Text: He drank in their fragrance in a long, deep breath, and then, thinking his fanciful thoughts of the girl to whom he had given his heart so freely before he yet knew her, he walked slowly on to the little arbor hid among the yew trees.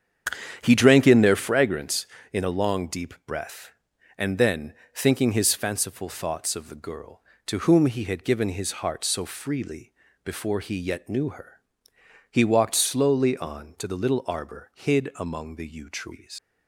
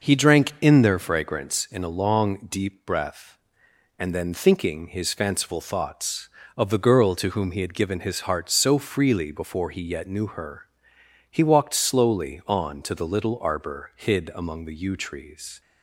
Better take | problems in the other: second | starts louder than the rest; strong; until 1.6 s; 9 dB // pauses between "freely" and "before"; slight; at 9.9 s; 0.32 s long // leaves "trees" unfinished; at 16.3 s; 125 ms

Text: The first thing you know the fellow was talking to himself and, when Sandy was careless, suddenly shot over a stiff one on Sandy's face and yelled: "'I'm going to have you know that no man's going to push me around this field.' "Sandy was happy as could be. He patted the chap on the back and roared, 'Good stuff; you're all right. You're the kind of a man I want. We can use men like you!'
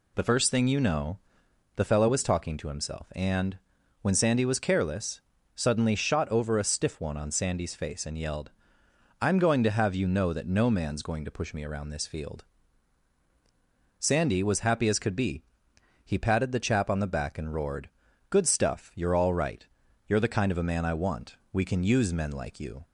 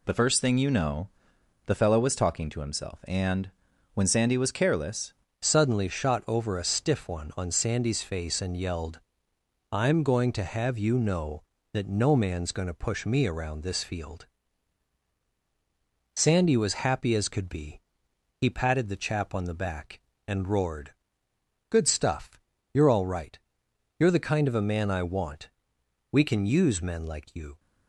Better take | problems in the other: first | pauses between "know" and "the"; noticeable; at 1.0 s; 0.58 s long; noticeable in the first // changes voice at "suddenly"; from 5.3 s on; 22.2 s long

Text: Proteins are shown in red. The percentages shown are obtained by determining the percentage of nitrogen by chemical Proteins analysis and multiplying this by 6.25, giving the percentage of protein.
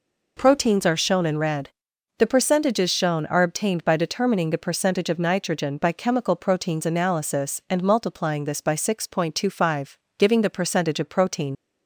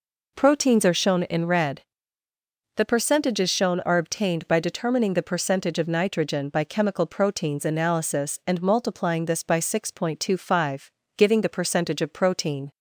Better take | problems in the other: second | leaves "protein" unfinished; at 11.5 s; 65 ms

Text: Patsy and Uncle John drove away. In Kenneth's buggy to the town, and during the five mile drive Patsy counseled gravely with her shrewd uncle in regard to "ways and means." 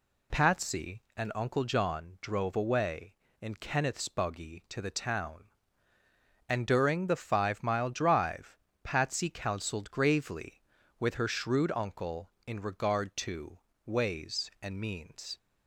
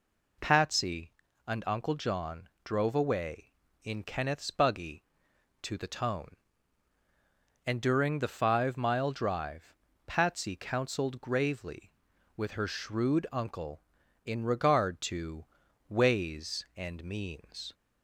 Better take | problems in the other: first | pauses between "John" and "drove"; slight; at 2.4 s; 0.16 s long // says "tone" for "town"; at 5.8 s // pauses between "drive" and "Patsy"; slight; at 9.7 s; 0.32 s long; slight in the first // pauses between "to" and "ways"; at 15.4 s; 0.42 s long; slight in the first

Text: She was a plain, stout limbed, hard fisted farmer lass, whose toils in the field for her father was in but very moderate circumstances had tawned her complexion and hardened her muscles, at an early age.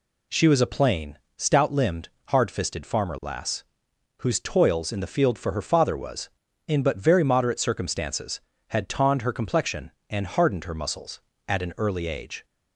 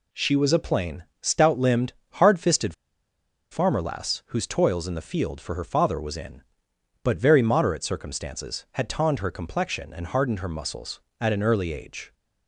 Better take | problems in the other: first | pauses between "fisted" and "farmer"; noticeable; at 2.7 s; 0.76 s long

